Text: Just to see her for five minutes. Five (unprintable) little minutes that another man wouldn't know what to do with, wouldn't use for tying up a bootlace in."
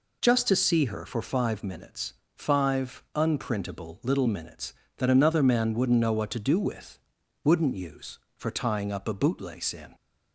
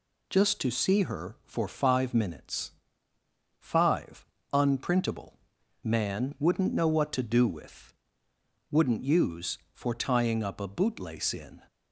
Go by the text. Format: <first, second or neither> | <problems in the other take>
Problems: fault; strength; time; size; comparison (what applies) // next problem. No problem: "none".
first | skips "little minutes that another"; at 5.6 s